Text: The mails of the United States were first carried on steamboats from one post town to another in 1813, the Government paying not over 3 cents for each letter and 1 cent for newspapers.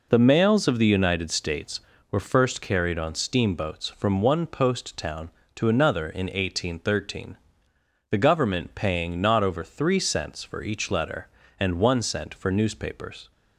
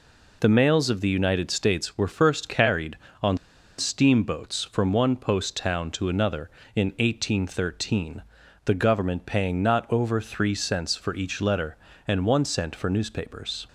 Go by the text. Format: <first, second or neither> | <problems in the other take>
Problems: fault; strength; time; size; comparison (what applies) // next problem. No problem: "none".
first | pauses between "on" and "steamboats"; at 3.3 s; 0.42 s long